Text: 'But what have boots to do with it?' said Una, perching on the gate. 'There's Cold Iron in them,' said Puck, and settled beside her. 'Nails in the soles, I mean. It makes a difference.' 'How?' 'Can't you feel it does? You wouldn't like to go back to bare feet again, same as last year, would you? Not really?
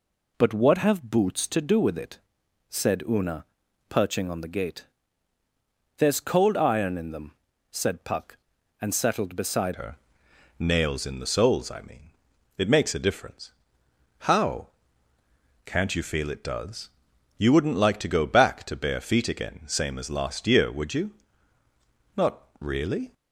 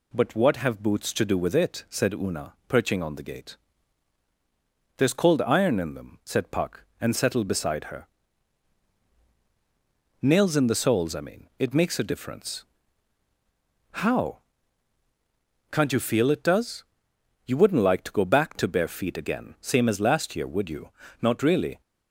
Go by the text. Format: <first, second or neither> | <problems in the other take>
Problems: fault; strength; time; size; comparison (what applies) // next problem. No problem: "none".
second | changes voice at "her"; from 9.7 s on; 13.4 s long // pauses between "Not" and "really"; slight; at 22.4 s; 0.16 s long